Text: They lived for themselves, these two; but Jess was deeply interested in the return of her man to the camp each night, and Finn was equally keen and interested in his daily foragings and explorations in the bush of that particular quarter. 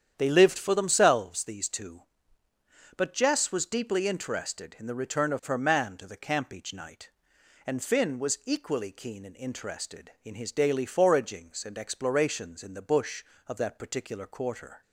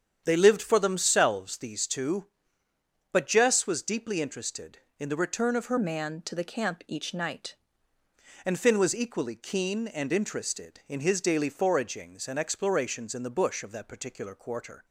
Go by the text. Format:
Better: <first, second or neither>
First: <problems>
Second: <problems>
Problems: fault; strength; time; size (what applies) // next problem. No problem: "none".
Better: first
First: starts louder than the rest; strong; until 1.1 s; 9 dB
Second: starts louder than the rest; strong; until 1.2 s; 8.5 dB // changes voice from "man" to "night"; from 5.7 to 7.5 s; 1.8 s long